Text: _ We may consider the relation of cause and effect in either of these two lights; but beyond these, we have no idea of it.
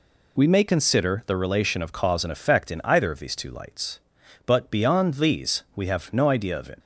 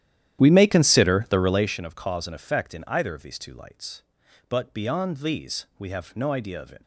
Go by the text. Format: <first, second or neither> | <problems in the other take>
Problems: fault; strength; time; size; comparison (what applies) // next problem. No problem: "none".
first | starts louder than the rest; strong; until 1.7 s; 11.5 dB